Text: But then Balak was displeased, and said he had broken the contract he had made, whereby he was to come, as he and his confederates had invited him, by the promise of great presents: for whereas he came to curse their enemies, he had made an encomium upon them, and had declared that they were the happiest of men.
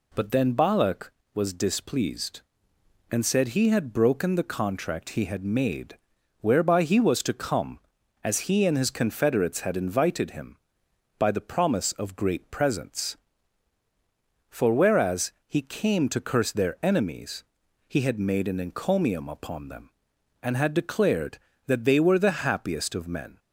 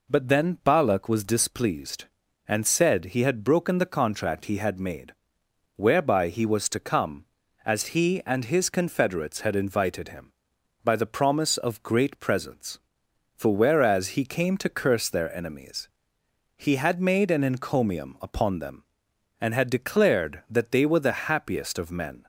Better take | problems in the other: neither | none

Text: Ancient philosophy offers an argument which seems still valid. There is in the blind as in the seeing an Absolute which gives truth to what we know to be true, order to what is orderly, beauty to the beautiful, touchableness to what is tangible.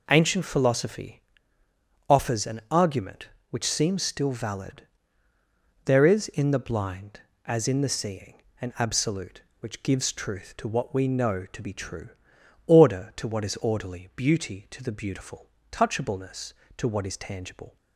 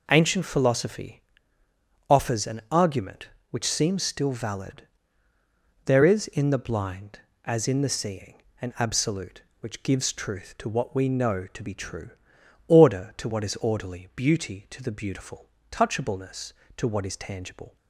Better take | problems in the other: neither | pauses between "philosophy" and "offers"; noticeable; the same in both // pauses between "seeing" and "an"; slight; the same in both

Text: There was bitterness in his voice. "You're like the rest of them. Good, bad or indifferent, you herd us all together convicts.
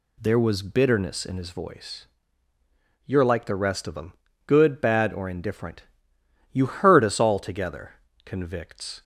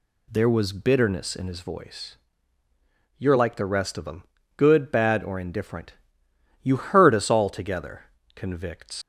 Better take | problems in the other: first | pauses between "together" and "convicts"; slight; at 8.0 s; 0.28 s long; slight in the first // leaves "convicts" unfinished; at 9.0 s; 115 ms

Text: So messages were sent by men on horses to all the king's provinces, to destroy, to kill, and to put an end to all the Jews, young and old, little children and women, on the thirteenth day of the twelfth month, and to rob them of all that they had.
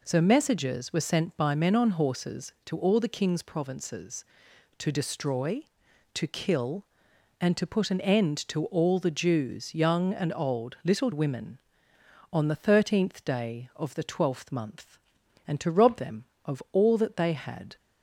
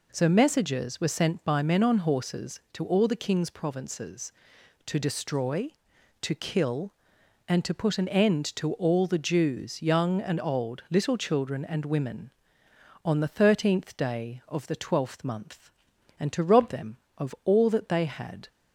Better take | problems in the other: second | skips "children and"; at 11.1 s

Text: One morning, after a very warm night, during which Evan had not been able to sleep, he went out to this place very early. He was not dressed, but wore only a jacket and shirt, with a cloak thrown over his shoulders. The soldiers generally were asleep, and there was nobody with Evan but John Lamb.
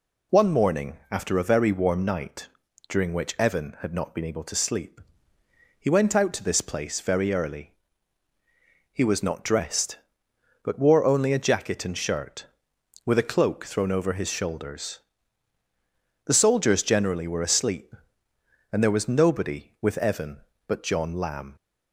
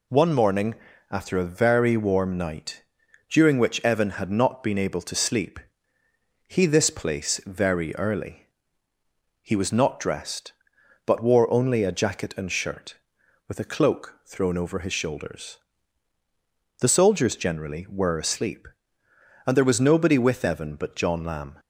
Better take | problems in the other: first | skips "went out to"; at 6.6 s

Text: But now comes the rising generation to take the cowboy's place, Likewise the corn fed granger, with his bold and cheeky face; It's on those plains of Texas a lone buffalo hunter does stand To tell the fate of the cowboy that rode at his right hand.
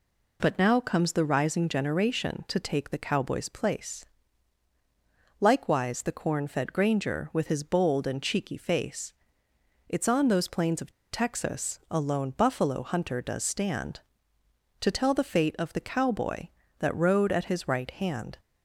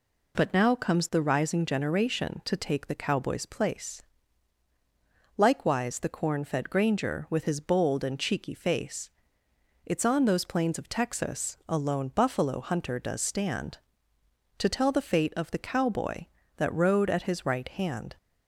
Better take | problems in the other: second | pauses between "of" and "Texas"; slight; at 10.9 s; 0.20 s long

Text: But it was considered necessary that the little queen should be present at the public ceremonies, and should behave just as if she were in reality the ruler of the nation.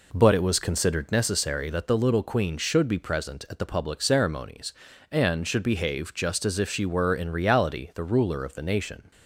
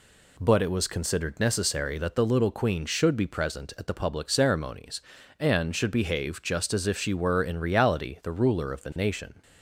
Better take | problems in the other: second | starts louder than the rest; until 1.2 s; 3.5 dB

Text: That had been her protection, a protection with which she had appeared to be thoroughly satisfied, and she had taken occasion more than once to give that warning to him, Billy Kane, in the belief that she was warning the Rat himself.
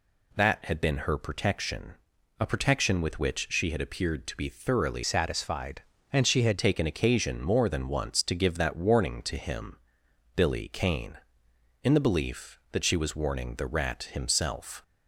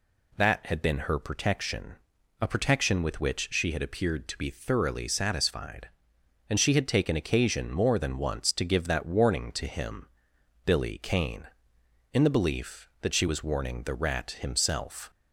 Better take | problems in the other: second | changes voice from "satisfied" to "had"; from 5.0 to 6.5 s; 1.5 s long

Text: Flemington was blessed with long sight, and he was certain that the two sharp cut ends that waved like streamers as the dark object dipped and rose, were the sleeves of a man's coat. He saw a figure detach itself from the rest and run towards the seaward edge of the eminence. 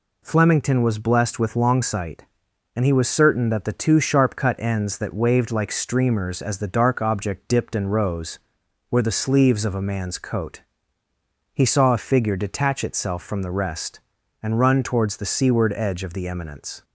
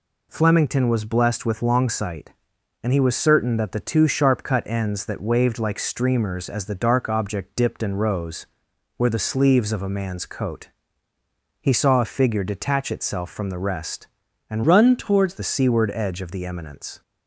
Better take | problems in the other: first | changes voice from "run" to "towards"; from 14.6 to 15.3 s; 0.7 s long

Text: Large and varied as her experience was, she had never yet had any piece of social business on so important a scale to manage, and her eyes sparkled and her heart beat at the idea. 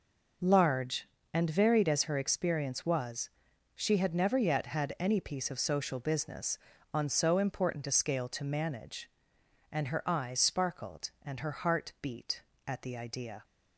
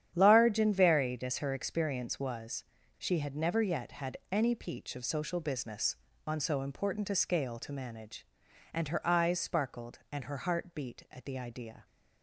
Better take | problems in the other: first | starts louder than the rest; strong; until 1.1 s; 9.5 dB // says "peach" for "piece"; at 4.5 s

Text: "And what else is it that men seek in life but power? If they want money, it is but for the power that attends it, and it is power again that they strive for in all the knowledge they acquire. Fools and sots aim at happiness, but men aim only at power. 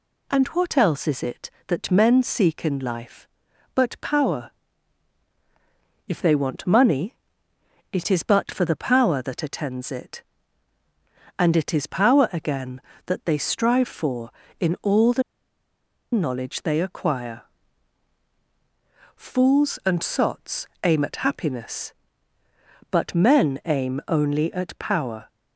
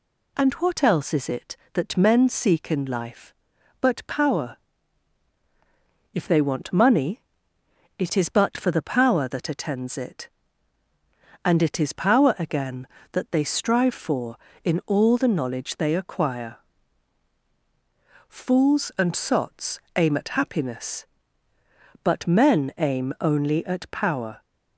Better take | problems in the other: second | pauses between "the" and "knowledge"; noticeable; at 15.2 s; 0.91 s long // pauses between "sots" and "aim"; slight; at 20.6 s; 0.18 s long; slight in the second

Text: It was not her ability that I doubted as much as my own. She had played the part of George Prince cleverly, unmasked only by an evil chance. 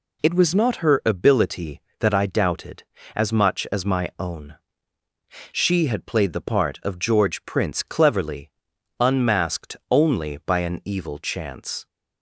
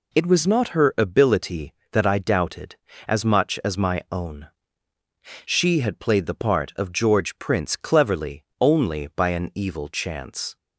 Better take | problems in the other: first | skips "unmasked"; at 8.5 s

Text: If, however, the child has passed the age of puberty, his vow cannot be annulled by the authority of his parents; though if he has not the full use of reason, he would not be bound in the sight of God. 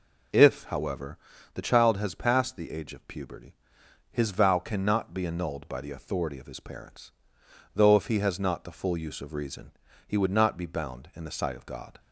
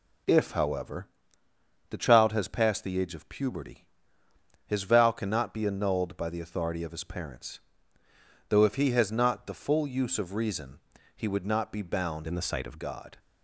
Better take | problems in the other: first | changes voice from "in" to "of"; from 12.2 to 12.8 s; 0.6 s long

